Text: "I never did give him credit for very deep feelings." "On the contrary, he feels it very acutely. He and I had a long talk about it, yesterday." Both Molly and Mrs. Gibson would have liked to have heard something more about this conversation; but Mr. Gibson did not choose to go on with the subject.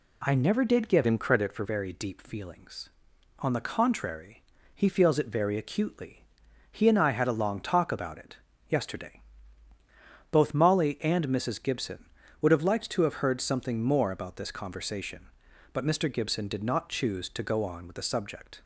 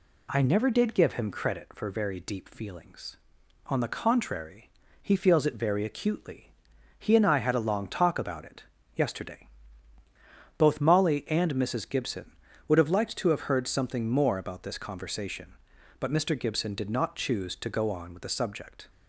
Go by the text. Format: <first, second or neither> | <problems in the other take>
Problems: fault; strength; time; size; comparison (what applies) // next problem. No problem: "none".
second | changes voice from "him" to "for"; from 1.0 to 1.6 s; 0.6 s long